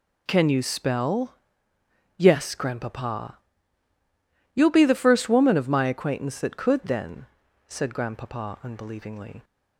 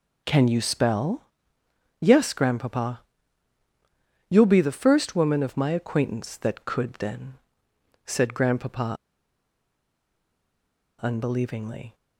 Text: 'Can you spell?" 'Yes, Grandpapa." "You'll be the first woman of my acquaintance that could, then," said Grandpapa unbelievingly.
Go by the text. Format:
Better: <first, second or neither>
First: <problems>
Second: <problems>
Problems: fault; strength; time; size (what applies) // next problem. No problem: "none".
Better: first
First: none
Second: pauses between "Grandpapa" and "unbelievingly"; strong; at 8.9 s; 2.0 s long